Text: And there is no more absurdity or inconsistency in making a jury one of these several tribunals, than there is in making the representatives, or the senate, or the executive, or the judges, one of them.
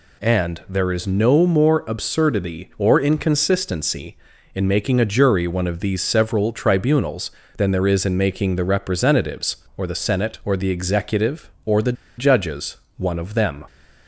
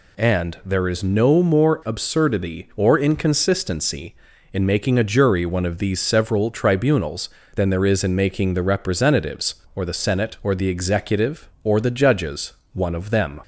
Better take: second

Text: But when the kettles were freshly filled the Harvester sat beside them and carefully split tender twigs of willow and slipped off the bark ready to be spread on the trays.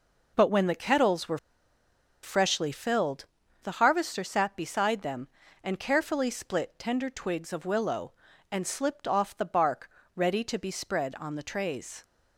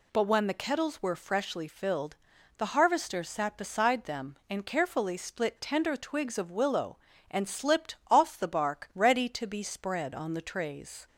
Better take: second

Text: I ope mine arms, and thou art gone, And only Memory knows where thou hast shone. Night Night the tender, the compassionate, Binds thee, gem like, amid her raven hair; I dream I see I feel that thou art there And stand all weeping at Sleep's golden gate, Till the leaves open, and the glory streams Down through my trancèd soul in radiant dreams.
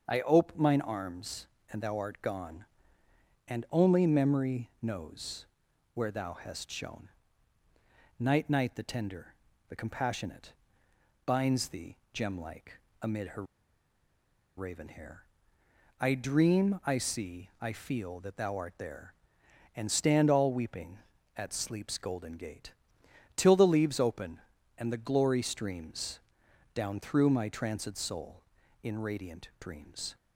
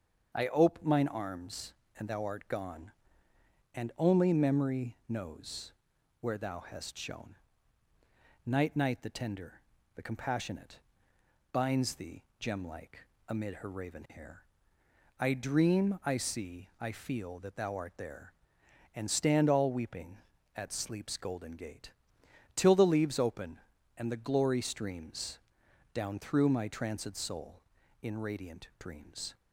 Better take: second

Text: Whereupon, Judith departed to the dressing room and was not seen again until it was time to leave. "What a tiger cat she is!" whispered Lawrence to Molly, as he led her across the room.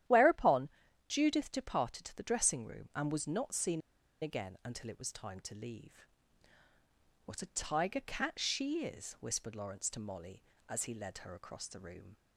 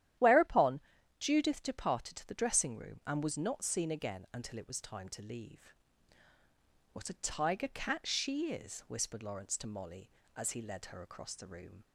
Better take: second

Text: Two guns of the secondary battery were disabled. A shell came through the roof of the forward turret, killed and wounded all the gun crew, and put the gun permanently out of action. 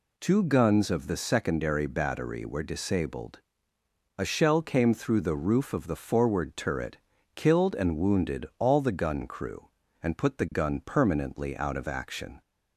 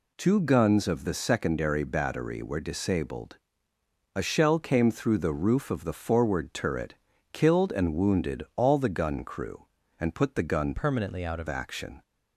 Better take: first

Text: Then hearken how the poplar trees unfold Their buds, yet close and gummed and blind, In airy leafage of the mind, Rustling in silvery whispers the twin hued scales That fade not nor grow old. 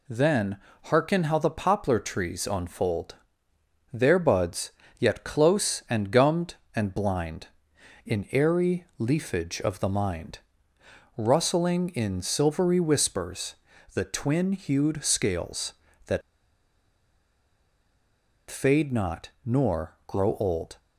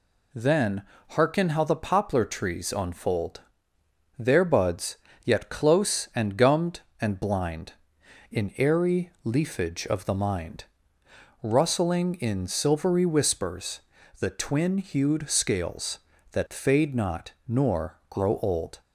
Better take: second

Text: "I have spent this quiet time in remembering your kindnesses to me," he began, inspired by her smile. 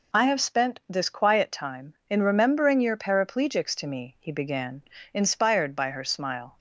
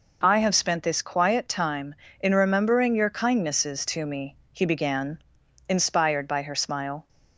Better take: second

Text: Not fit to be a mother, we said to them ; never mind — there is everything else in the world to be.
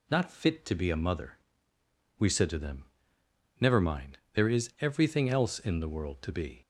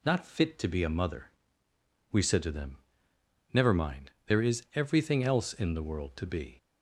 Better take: neither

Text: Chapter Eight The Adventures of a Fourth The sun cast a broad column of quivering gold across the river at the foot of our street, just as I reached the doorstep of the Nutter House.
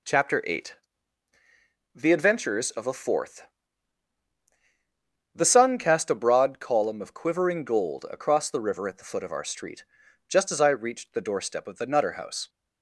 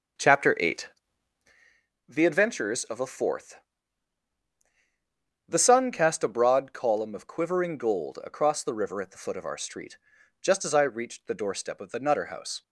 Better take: first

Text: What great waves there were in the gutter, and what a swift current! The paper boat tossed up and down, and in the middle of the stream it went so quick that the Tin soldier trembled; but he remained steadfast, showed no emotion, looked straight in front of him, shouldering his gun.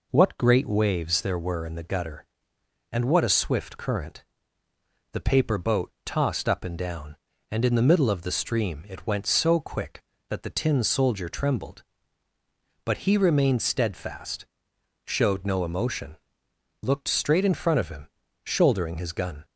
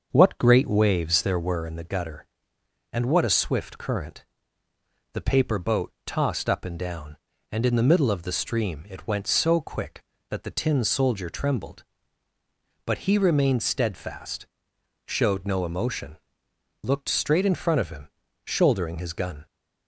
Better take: first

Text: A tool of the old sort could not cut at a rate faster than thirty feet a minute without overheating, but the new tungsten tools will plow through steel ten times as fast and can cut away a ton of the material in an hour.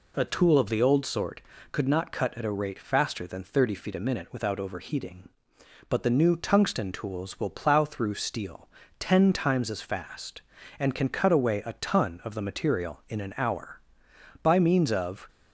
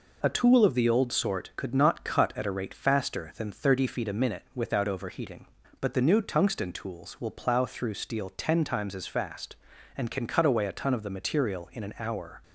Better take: second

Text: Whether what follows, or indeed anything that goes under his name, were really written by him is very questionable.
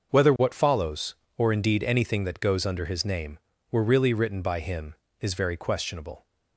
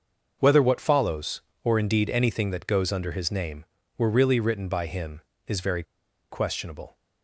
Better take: first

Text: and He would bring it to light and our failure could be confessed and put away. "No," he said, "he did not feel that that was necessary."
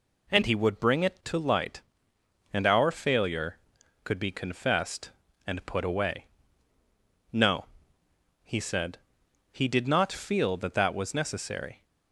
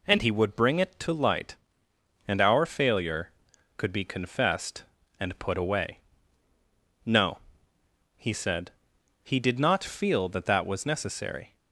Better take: neither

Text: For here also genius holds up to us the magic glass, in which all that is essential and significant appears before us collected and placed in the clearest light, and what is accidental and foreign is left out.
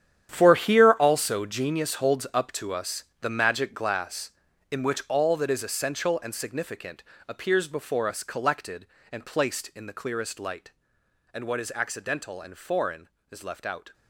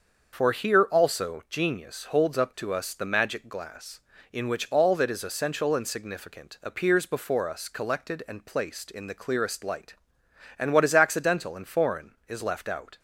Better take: second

